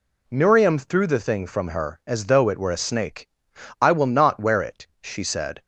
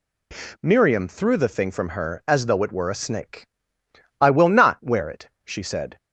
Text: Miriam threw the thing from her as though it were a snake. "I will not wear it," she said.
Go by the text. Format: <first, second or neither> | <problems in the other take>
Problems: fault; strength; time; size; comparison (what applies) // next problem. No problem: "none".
neither | none